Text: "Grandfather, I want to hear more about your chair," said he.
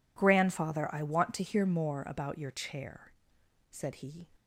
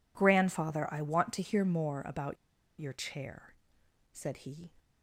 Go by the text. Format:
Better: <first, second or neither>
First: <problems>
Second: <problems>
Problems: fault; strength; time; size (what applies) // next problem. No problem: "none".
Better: first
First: none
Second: pauses between "about" and "your"; at 2.3 s; 0.44 s long